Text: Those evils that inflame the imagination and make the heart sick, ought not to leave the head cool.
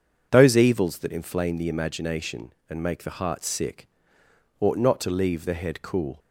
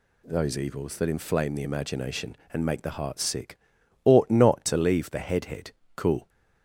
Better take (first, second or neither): first